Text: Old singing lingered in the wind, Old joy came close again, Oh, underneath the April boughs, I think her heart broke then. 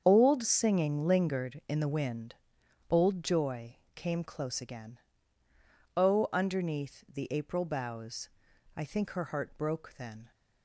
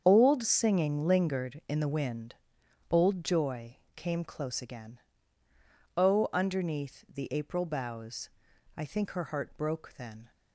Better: neither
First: starts louder than the rest; strong; until 1.0 s; 7.5 dB // pauses between "joy" and "came"; slight; at 3.7 s; 0.18 s long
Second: starts louder than the rest; strong; until 1.0 s; 7.5 dB // pauses between "joy" and "came"; slight; at 3.7 s; 0.18 s long

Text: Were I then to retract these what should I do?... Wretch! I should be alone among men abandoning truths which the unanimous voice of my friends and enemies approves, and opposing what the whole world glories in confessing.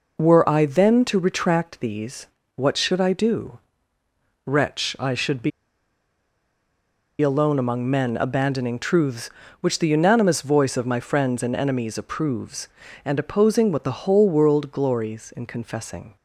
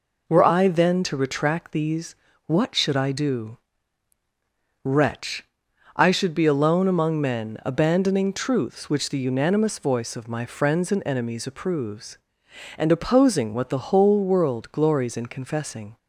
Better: second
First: pauses between "these" and "what"; slight; at 2.2 s; 0.30 s long // pauses between "be" and "alone"; strong; at 5.5 s; 1.7 s long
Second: pauses between "these" and "what"; slight; at 2.1 s; 0.32 s long

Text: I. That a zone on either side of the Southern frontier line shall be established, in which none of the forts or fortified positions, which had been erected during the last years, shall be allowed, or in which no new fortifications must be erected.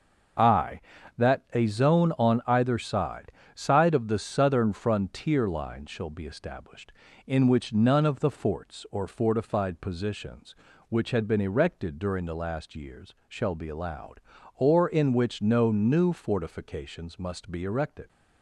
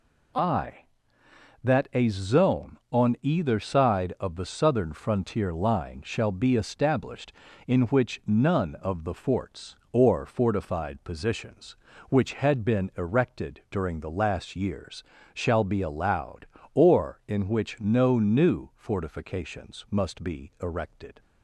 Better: second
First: starts louder than the rest; until 1.8 s; 6.5 dB // says "side" twice; at 3.5 s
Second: none

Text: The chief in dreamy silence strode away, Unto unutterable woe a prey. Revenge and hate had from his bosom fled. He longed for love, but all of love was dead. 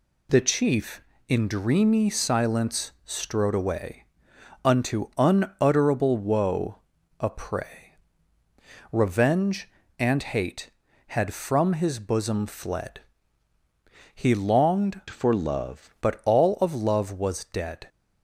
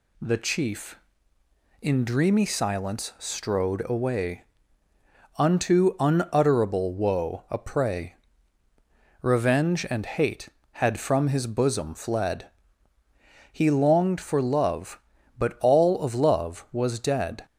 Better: second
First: pauses between "woe" and "a"; at 6.7 s; 0.40 s long // changes voice from "for" to "love"; from 15.0 to 15.9 s; 0.9 s long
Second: none

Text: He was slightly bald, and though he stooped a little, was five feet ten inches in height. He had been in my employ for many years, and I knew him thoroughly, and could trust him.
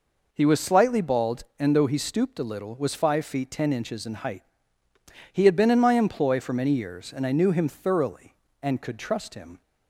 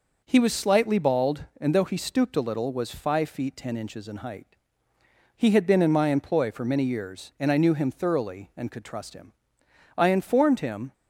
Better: first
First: none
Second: goes on to say "I informed him"; noticeable; from 9.9 s on; 0.96 s long

